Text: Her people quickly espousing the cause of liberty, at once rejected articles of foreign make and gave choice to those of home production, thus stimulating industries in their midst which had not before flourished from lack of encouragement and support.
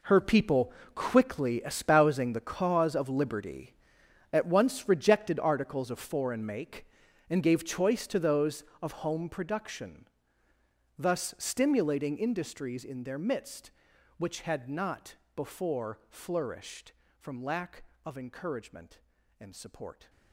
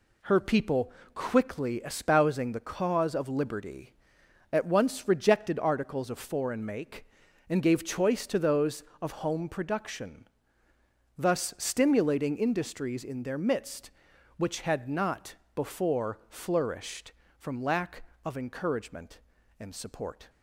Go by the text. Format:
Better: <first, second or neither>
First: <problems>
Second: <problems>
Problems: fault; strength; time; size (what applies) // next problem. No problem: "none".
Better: second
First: gets quieter; strong; throughout; 14 dB // pauses between "people" and "quickly"; slight; at 0.7 s; 0.22 s long // pauses between "not" and "before"; slight; at 15.1 s; 0.20 s long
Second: pauses between "people" and "quickly"; slight; at 0.9 s; 0.22 s long // pauses between "not" and "before"; slight; at 15.3 s; 0.20 s long